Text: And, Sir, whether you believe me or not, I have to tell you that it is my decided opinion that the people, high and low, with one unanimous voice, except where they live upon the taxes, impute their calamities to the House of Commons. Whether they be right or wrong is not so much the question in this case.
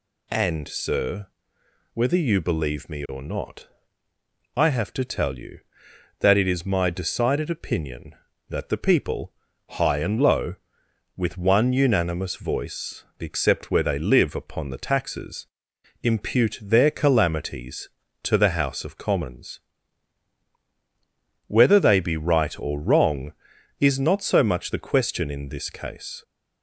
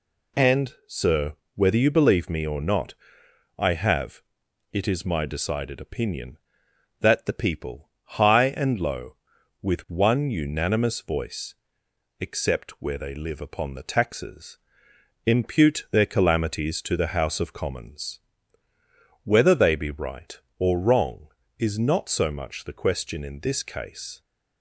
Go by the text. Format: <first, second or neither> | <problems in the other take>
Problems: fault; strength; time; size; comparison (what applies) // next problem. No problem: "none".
first | skips "to tell you that"; at 4.4 s